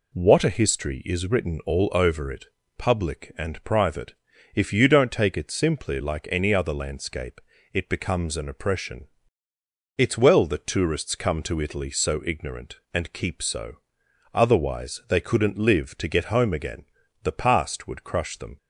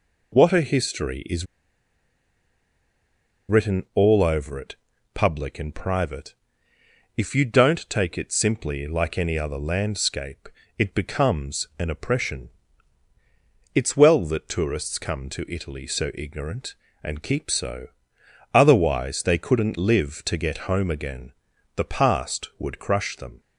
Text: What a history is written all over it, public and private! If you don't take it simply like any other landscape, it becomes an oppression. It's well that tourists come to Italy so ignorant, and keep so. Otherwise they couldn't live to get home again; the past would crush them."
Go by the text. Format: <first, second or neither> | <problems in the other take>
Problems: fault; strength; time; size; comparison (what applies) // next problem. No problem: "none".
first | pauses between "is" and "written"; strong; at 1.4 s; 2.0 s long